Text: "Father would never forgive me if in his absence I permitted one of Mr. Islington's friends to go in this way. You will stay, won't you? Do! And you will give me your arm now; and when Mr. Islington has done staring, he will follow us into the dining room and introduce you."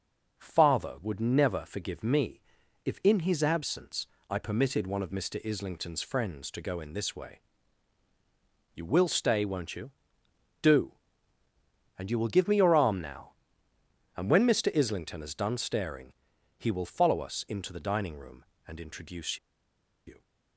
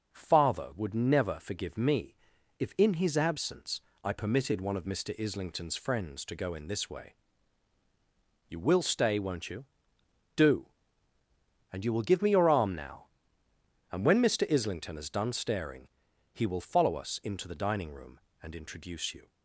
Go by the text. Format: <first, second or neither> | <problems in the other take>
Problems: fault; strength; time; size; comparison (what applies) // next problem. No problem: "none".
second | starts louder than the rest; noticeable; until 1.4 s; 6 dB; also in the second // pauses between "me" and "if"; at 2.4 s; 0.44 s long; also in the second // pauses between "absence" and "I"; slight; at 4.0 s; 0.24 s long; slight in the second // pauses between "introduce" and "you"; noticeable; at 19.3 s; 0.69 s long